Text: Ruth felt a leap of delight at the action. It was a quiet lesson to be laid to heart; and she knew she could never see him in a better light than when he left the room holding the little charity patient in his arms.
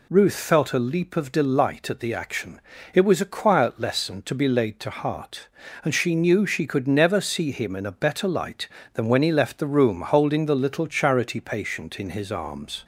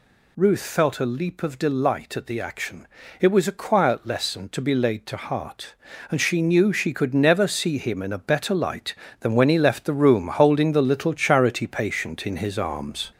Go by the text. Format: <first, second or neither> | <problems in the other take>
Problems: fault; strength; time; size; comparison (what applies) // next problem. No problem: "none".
first | gets louder; noticeable; throughout; 4.5 dB